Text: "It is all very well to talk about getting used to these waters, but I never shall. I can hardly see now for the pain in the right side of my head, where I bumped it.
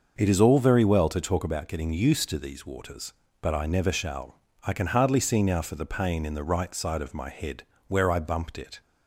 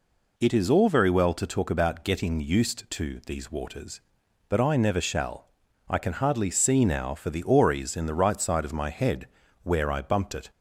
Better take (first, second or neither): first